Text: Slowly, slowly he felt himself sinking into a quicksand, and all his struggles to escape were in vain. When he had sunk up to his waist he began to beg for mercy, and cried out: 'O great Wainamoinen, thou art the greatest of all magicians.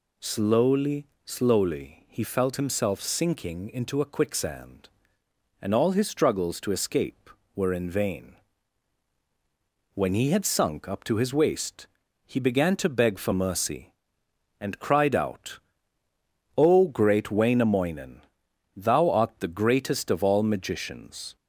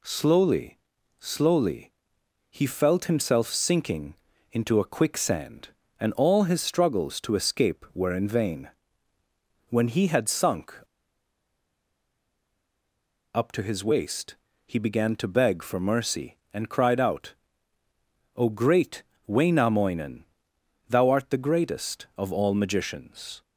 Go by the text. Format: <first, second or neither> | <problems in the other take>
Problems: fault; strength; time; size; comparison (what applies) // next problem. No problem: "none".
first | pauses between "slowly" and "he"; noticeable; at 1.9 s; 0.58 s long // pauses between "sinking" and "into"; slight; at 4.1 s; 0.36 s long // pauses between "sunk" and "up"; strong; at 10.7 s; 2.6 s long // pauses between "waist" and "he"; slight; at 14.3 s; 0.30 s long; also in the first // pauses between "great" and "Wainamoinen"; slight; at 19.0 s; 0.22 s long